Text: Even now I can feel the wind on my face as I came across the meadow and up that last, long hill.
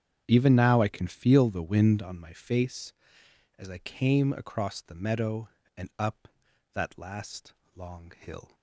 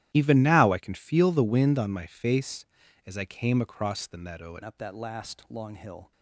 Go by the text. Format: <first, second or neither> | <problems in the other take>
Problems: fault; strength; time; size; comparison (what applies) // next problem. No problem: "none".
first | starts louder than the rest; strong; until 1.1 s; 13.5 dB; strong in the first // changes voice at "up"; from 4.6 s on; 1.5 s long